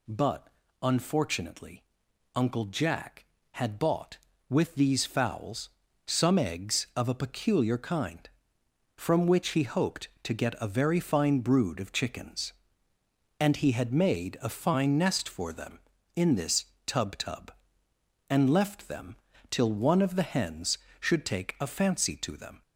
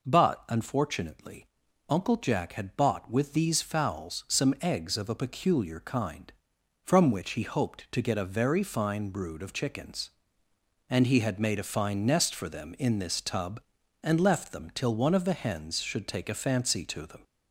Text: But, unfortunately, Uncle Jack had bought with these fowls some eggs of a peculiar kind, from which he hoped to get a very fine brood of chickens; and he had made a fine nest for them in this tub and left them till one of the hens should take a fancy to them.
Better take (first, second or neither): second